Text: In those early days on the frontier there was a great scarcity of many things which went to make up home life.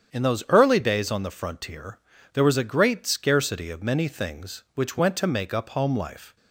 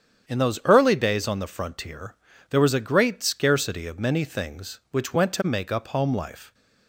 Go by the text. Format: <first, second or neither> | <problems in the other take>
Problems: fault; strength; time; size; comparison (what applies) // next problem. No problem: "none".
neither | starts louder than the rest; strong; the same in both // pauses between "frontier" and "there"; slight; the same in both